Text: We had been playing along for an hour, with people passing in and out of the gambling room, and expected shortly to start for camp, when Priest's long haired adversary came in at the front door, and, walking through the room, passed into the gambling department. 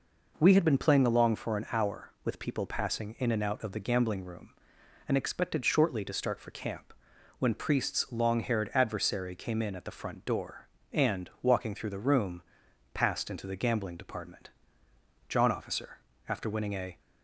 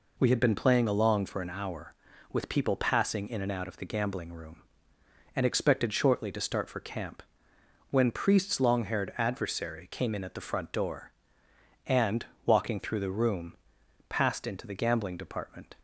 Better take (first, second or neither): second